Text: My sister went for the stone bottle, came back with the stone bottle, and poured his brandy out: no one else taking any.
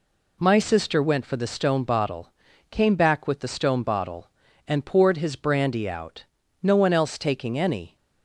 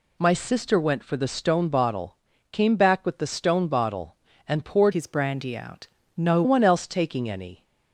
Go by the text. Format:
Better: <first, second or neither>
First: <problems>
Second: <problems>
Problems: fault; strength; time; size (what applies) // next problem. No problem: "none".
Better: first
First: none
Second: changes voice from "his" to "no"; from 4.9 to 6.4 s; 1.5 s long